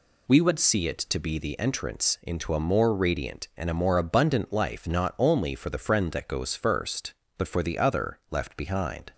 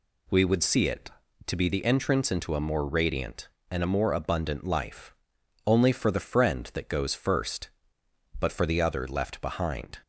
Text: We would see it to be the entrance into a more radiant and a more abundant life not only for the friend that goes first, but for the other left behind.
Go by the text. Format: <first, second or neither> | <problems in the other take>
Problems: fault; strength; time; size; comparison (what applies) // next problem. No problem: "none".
first | skips "not"; at 5.3 s